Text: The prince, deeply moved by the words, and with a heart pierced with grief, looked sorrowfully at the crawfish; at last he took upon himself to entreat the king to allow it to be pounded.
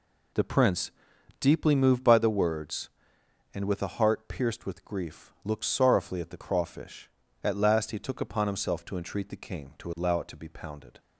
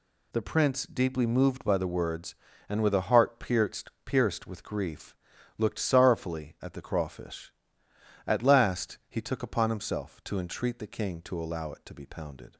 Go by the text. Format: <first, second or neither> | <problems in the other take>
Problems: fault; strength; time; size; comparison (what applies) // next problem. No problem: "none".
first | says "pierced" twice; at 4.0 s